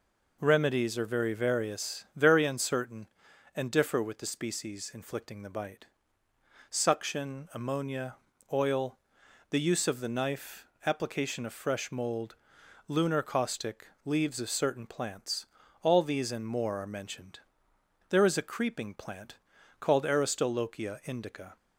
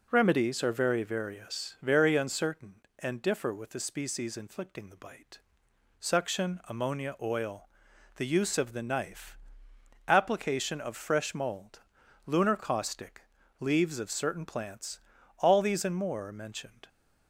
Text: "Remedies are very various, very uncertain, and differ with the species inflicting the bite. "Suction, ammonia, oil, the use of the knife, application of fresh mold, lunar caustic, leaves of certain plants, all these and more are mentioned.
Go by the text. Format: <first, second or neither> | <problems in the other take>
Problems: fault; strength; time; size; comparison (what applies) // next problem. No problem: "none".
second | goes on to say "There is a creeping plant called Aristolochia indica"; strong; from 18.1 s on; 3.4 s long